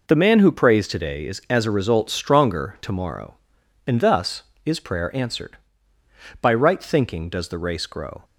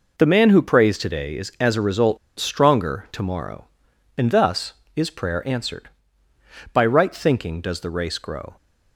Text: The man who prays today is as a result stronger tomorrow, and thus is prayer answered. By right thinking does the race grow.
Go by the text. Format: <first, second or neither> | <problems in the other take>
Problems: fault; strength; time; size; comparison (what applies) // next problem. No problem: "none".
first | pauses between "result" and "stronger"; slight; at 2.1 s; 0.22 s long